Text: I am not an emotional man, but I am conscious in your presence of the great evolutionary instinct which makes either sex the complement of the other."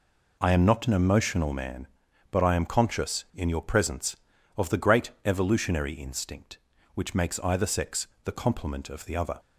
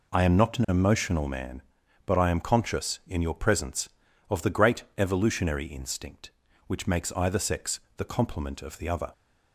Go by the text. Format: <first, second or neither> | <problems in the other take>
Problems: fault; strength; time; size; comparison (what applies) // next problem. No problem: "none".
neither | pauses between "great" and "evolutionary"; slight; the same in both // pauses between "sex" and "the"; slight; the same in both